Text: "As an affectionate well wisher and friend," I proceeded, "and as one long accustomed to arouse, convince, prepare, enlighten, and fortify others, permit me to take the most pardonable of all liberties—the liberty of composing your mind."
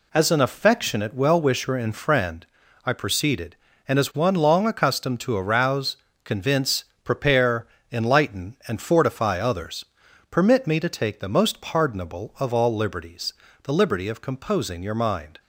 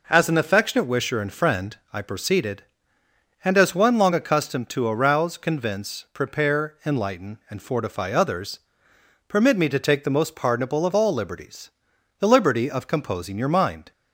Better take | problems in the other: first | skips "well"; at 0.8 s

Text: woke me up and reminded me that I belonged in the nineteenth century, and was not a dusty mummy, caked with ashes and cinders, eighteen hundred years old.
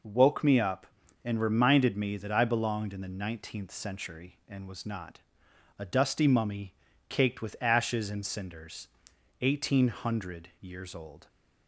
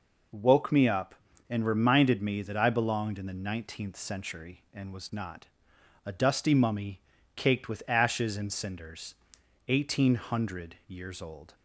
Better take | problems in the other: neither | pauses between "not" and "a"; noticeable; the same in both

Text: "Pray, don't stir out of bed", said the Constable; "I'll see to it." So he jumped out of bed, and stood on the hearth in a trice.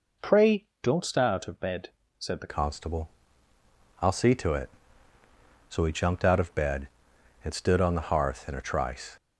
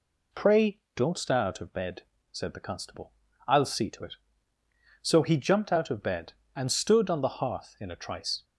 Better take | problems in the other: second | changes voice at "Constable"; from 2.4 s on; 6.7 s long

